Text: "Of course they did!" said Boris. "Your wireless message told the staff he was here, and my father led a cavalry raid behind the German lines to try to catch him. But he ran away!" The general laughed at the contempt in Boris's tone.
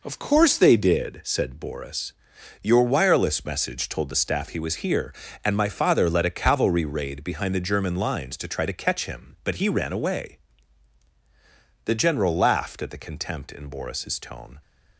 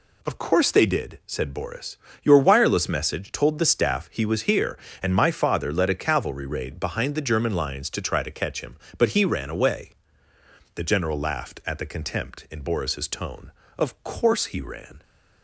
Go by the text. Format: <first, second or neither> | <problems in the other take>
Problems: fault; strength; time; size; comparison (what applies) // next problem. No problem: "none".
first | goes on to say "Of course he ran"; noticeable; from 13.7 s on; 1.2 s long